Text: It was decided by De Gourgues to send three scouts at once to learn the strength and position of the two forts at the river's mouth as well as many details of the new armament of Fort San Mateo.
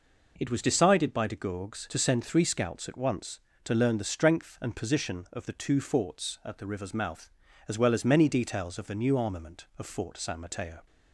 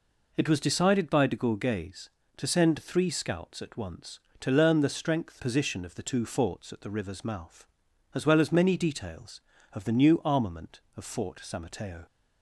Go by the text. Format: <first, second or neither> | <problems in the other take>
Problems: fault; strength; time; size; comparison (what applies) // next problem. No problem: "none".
first | skips "and"; at 5.4 s